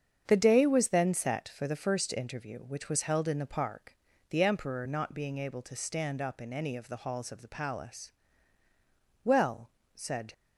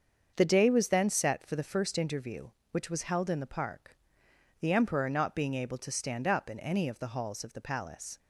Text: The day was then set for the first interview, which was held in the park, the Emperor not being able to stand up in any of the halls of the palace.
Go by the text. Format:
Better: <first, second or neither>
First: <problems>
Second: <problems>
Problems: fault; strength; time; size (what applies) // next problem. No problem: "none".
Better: second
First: starts louder than the rest; strong; until 1.2 s; 7.5 dB // goes on to say "Well said"; noticeable; from 9.2 s on; 1.1 s long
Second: starts louder than the rest; until 1.3 s; 6.5 dB